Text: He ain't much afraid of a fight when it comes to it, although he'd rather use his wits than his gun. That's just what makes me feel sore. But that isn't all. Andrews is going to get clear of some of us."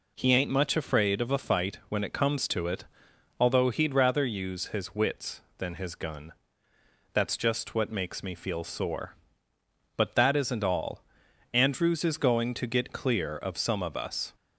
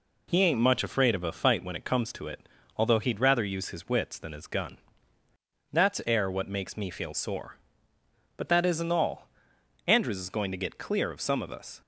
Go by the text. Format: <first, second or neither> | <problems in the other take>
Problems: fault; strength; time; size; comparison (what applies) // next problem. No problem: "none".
first | says "air" for "just"; at 6.0 s